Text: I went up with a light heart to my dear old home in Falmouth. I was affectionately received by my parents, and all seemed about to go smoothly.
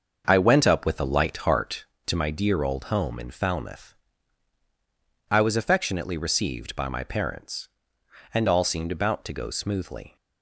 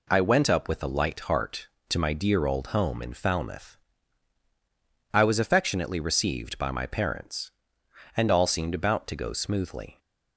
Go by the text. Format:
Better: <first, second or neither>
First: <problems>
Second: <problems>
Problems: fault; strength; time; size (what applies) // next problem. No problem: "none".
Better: second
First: starts louder than the rest; until 2.0 s; 6.5 dB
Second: none